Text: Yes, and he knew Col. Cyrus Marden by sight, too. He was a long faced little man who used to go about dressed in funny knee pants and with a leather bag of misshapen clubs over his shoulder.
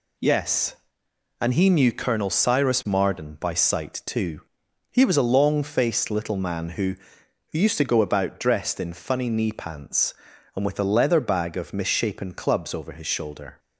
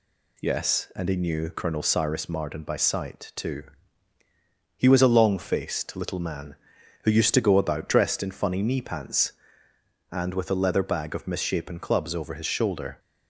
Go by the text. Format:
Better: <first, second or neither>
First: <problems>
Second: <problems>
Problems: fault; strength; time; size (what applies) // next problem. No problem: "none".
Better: second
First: says "who" twice; at 7.5 s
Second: none